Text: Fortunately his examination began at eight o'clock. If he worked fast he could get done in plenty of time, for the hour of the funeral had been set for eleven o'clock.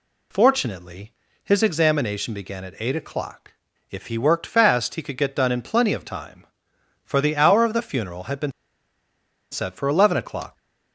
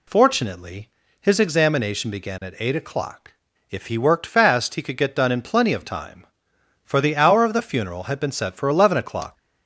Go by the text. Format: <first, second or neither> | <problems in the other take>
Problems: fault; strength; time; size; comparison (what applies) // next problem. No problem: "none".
second | pauses between "Fortunately" and "his"; slight; at 1.1 s; 0.32 s long; slight in the second // pauses between "been" and "set"; at 8.5 s; 1.0 s long